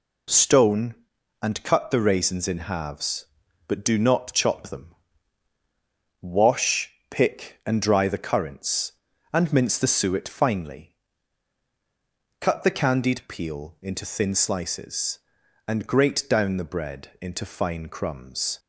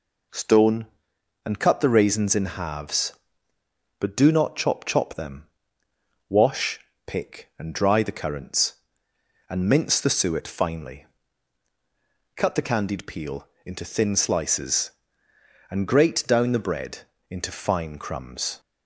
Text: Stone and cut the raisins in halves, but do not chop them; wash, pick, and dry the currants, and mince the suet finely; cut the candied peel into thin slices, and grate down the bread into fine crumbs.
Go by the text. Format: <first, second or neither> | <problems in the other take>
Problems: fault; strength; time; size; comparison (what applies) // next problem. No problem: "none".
first | says "chop" twice; at 4.8 s // pauses between "peel" and "into"; slight; at 13.4 s; 0.16 s long // pauses between "bread" and "into"; slight; at 16.9 s; 0.32 s long